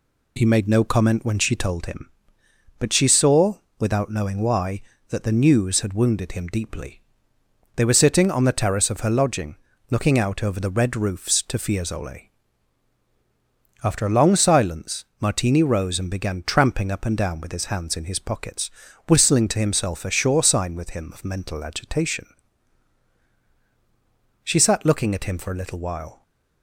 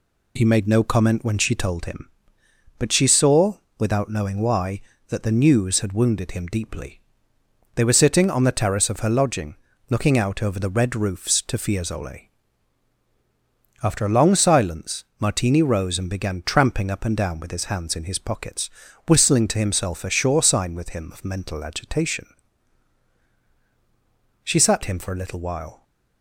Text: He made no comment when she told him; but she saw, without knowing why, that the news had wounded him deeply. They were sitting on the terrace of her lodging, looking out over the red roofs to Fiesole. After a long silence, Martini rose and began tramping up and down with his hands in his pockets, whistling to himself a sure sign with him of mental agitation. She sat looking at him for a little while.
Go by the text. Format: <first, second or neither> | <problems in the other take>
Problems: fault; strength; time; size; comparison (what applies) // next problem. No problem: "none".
first | skips "looking at"; at 24.8 s